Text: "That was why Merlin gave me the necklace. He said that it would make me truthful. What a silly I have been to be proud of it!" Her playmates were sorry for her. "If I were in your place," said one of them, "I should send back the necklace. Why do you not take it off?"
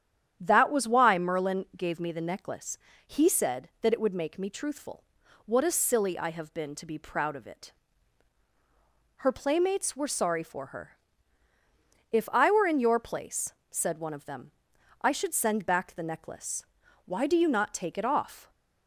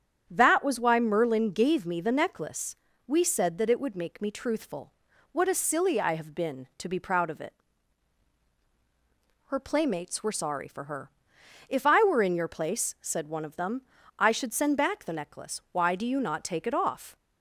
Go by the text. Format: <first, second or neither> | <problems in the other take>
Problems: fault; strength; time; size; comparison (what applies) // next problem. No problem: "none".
first | starts louder than the rest; strong; until 1.2 s; 8.5 dB; strong in the first // says "We" for "He"; at 3.0 s